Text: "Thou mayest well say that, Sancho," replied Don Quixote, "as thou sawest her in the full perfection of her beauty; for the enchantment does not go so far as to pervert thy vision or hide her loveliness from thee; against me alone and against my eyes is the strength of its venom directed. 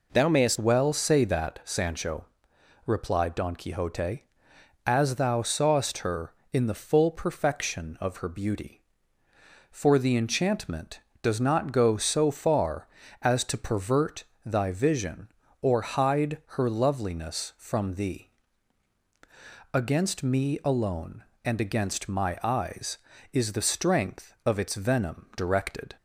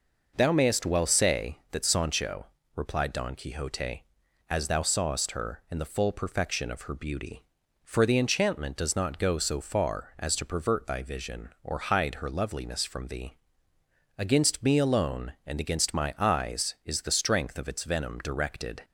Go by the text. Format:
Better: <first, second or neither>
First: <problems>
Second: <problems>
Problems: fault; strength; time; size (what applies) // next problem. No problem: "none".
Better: second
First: changes voice at "well"; from 0.5 s on; 25.4 s long // pauses between "pervert" and "thy"; slight; at 14.2 s; 0.22 s long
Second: none